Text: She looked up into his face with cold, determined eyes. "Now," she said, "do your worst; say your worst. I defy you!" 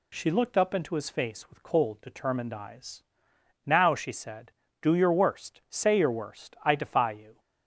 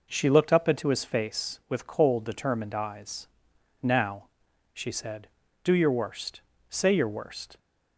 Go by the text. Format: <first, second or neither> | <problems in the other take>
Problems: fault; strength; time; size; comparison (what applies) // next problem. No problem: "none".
first | stops before "I defy you"; at 7.5 s